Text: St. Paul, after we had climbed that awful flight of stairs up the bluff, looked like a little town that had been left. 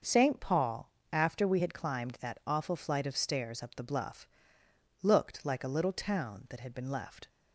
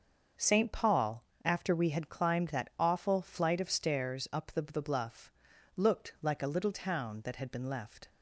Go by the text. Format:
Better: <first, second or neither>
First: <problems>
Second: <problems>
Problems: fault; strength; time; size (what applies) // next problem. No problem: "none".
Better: first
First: starts louder than the rest; until 1.3 s; 6.5 dB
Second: starts louder than the rest; until 1.6 s; 6.5 dB // says "the" twice; at 4.6 s